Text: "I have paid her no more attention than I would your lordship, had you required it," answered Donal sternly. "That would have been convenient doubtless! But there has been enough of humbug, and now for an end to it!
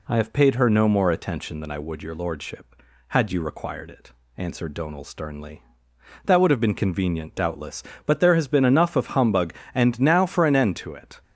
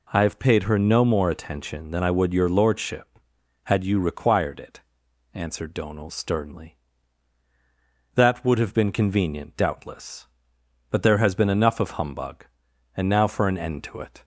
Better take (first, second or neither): neither